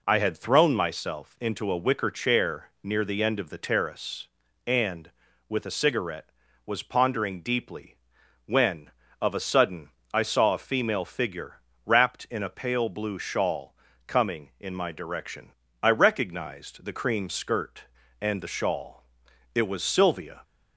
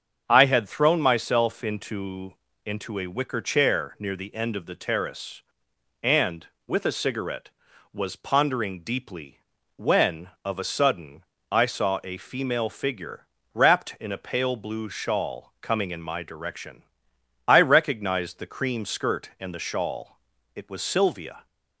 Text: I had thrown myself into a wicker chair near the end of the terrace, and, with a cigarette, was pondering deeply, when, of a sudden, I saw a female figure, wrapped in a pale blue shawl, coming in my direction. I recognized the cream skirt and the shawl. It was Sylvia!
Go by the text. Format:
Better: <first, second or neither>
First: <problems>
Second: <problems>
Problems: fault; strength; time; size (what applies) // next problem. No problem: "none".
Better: first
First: none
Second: starts louder than the rest; until 1.2 s; 7 dB // says "into" twice; at 2.6 s